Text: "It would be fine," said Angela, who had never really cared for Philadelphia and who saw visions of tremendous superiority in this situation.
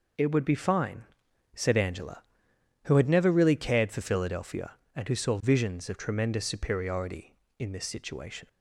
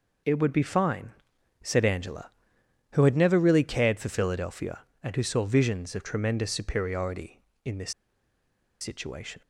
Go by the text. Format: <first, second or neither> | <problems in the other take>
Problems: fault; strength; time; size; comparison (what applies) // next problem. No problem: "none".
first | pauses between "this" and "situation"; noticeable; at 7.9 s; 0.89 s long